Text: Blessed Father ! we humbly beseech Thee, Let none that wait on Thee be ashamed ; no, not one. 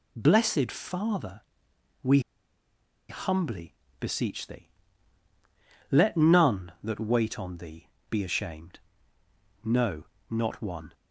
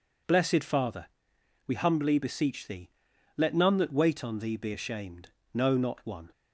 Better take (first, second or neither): second